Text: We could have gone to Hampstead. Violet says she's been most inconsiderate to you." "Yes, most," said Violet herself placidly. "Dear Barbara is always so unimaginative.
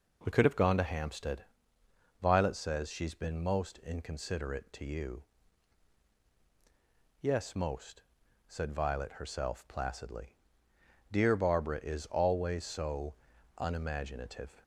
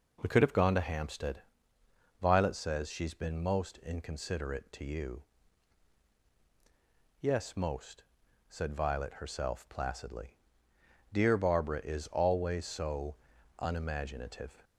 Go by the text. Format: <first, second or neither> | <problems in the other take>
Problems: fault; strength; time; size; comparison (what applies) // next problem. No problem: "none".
neither | pauses between "so" and "unimaginative"; the same in both